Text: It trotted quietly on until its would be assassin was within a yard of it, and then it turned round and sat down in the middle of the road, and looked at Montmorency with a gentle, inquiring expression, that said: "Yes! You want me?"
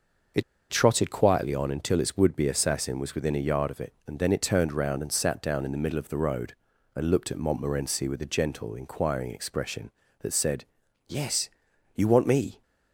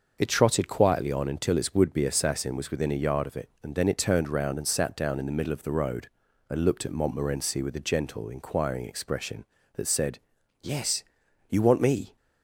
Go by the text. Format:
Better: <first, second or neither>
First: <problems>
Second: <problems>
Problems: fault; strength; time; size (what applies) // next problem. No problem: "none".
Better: second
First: starts louder than the rest; until 1.6 s; 6.5 dB // pauses between "It" and "trotted"; slight; at 0.4 s; 0.28 s long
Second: starts louder than the rest; until 1.1 s; 6 dB